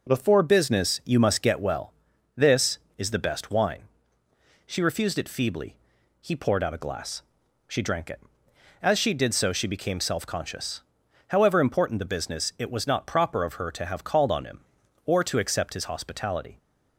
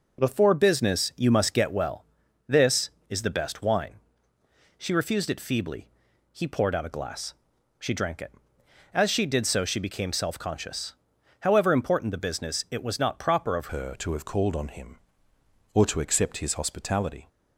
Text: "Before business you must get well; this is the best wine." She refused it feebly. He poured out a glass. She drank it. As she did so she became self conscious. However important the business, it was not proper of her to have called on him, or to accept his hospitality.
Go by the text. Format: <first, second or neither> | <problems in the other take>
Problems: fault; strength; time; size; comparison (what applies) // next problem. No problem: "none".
first | changes voice at "her"; from 13.7 s on; 3.5 s long